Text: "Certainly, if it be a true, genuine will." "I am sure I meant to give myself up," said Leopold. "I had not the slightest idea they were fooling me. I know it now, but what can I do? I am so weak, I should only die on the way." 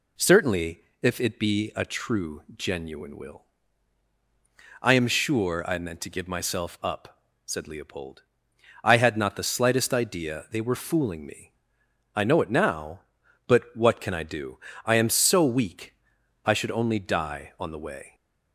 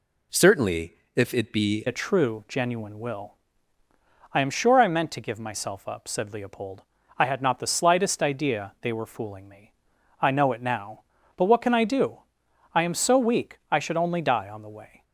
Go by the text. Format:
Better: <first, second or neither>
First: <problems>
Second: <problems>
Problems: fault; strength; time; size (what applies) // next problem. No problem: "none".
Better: first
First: none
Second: changes voice at "a"; from 1.8 s on; 13.2 s long